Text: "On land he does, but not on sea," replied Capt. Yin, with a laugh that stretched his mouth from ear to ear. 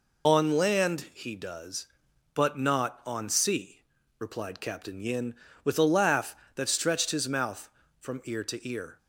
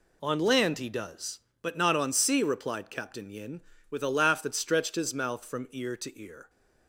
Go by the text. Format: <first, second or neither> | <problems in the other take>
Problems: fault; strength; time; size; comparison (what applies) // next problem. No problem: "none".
second | loses the start of "On"; at 0.2 s; 45 ms